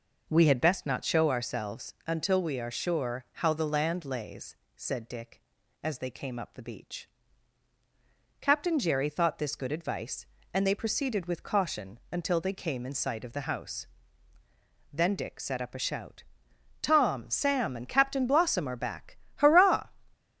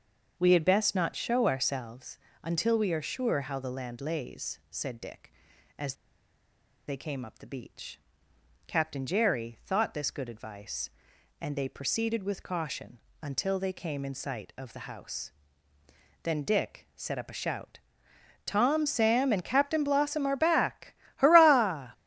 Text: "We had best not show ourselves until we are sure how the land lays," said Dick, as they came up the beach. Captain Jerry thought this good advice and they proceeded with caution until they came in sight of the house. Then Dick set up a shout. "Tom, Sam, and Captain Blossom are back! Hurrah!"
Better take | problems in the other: first | starts louder than the rest; until 1.3 s; 6.5 dB // pauses between "ourselves" and "until"; slight; at 2.1 s; 0.26 s long // pauses between "as" and "they"; noticeable; at 5.9 s; 0.94 s long // pauses between "caution" and "until"; slight; at 12.9 s; 0.22 s long

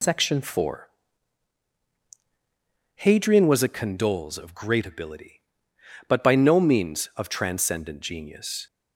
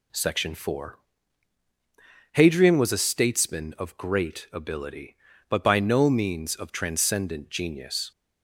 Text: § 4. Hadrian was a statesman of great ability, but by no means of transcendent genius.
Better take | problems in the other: second | says "condoles" for "statesman"; at 3.6 s

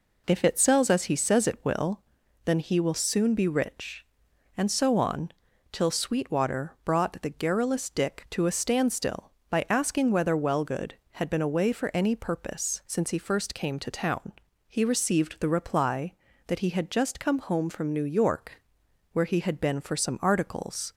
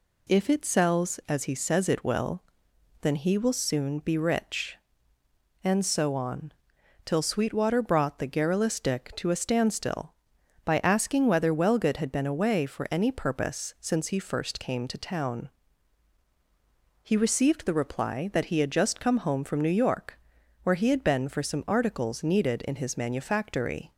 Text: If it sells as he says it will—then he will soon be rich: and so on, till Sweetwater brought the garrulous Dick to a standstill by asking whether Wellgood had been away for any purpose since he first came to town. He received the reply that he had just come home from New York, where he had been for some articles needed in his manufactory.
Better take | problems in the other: second | stops before "needed in his manufactory"; at 20.9 s

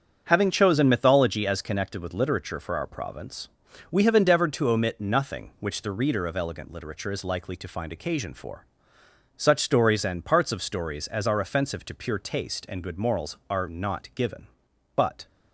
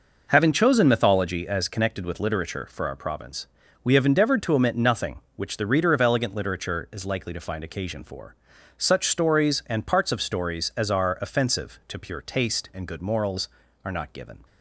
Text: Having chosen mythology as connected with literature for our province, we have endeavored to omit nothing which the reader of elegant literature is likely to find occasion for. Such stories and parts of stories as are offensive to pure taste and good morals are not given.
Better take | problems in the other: second | starts louder than the rest; until 1.2 s; 7 dB // goes on to say "But"; slight; from 14.9 s on; 0.30 s long

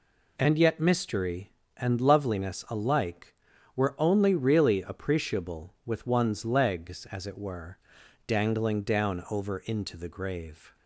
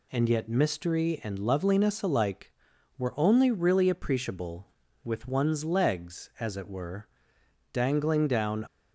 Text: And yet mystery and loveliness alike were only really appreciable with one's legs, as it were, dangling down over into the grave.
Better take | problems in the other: first | stops before "over into the grave"; at 8.6 s

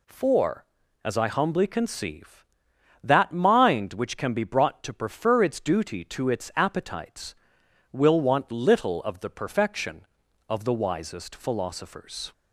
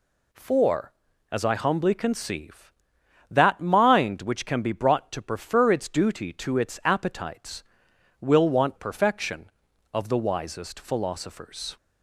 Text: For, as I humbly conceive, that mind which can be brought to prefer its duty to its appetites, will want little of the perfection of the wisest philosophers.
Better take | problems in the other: first | skips "little of the"; at 8.7 s

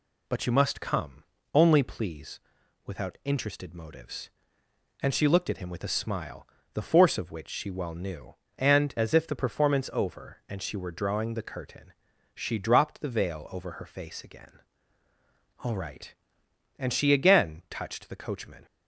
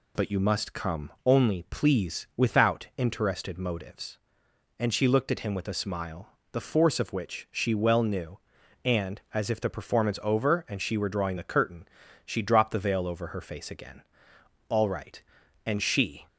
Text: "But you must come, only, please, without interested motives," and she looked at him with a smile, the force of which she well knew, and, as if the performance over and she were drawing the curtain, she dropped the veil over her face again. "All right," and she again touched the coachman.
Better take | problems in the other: first | stops before "again touched the coachman"; at 16.2 s

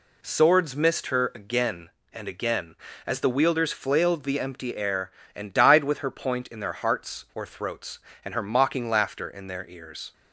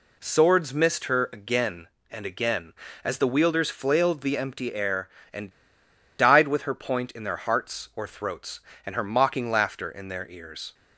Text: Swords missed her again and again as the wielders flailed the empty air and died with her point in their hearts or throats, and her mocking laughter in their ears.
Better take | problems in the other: first | pauses between "and" and "died"; noticeable; at 5.5 s; 0.66 s long

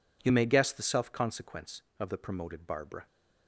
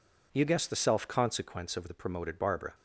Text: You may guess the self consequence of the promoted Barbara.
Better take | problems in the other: first | skips "may"; at 0.4 s

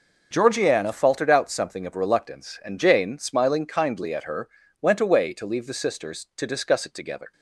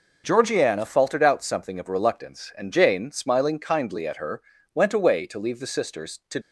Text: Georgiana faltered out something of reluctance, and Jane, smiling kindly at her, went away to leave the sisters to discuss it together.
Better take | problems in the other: first | stops before "discuss it together"; at 6.4 s

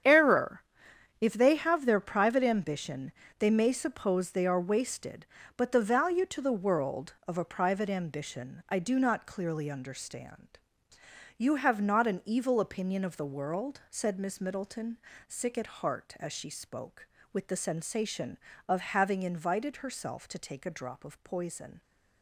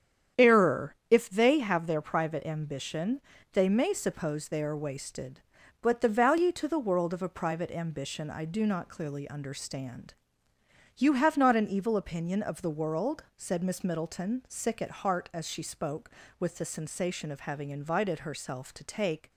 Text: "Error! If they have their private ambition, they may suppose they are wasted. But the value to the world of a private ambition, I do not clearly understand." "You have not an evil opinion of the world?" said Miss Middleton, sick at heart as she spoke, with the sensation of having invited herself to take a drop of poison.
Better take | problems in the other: first | starts louder than the rest; strong; until 1.5 s; 9 dB; strong in the first // stops before "a drop of poison"; at 19.3 s

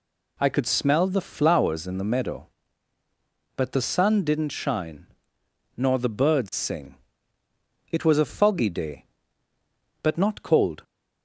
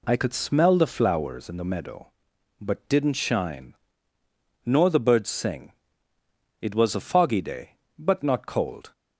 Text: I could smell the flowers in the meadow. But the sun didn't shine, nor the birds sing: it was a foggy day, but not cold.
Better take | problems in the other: first | skips "the sun"; at 2.8 s

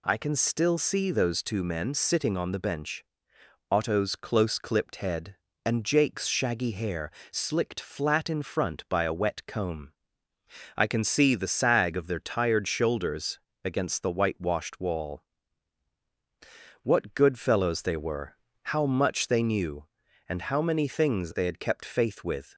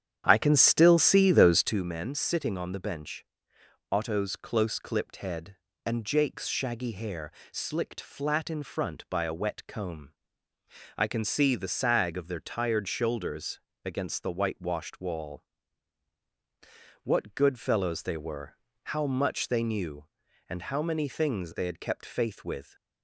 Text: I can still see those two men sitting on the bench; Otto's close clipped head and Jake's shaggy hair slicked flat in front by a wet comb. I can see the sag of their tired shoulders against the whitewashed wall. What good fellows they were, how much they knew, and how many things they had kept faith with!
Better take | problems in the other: first | starts louder than the rest; strong; until 1.9 s; 9.5 dB // pauses between "hair" and "slicked"; slight; at 7.3 s; 0.20 s long; slight in the first // pauses between "shoulders" and "against"; slight; at 13.5 s; 0.26 s long; slight in the first

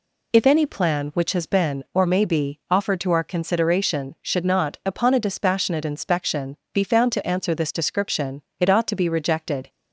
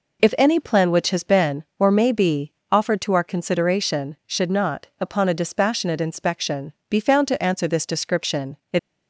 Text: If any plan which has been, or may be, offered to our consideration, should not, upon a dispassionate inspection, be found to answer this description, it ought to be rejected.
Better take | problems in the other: first | stops before "ought to be rejected"; at 8.7 s

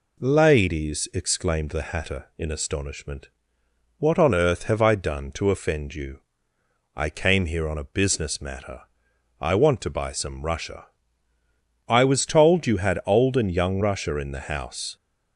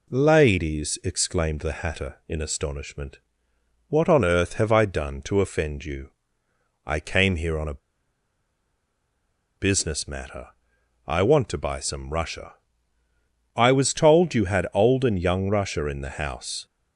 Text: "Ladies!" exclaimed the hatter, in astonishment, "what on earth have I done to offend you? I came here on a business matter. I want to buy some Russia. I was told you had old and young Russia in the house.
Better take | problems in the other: first | pauses between "a" and "business"; strong; at 7.7 s; 1.7 s long

